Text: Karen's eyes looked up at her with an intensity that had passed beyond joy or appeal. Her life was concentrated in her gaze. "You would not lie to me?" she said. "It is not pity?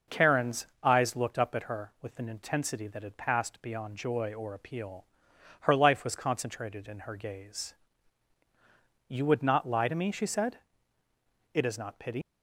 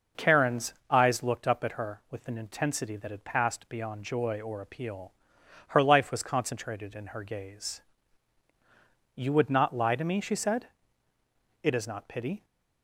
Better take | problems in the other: second | pauses between "Karen's" and "eyes"; slight; at 0.6 s; 0.18 s long; slight in the second // leaves "pity" unfinished; at 12.2 s; 135 ms

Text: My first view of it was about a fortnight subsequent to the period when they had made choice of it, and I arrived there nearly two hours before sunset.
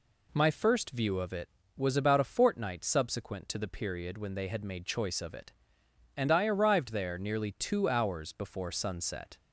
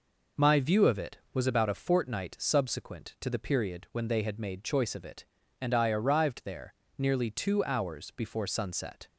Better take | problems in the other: first | skips "first"; at 0.5 s // pauses between "there" and "nearly"; slight; at 6.7 s; 0.24 s long

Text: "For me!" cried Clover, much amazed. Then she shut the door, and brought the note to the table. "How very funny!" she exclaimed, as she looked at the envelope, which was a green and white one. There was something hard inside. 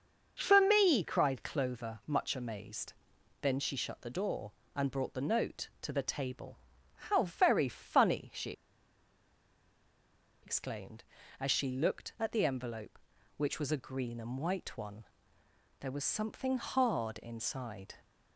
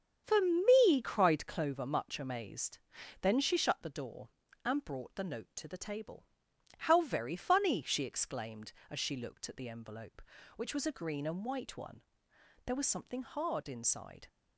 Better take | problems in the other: second | starts louder than the rest; until 1.3 s; 6.5 dB; strong in the second // pauses between "she" and "exclaimed"; strong; at 8.5 s; 1.9 s long

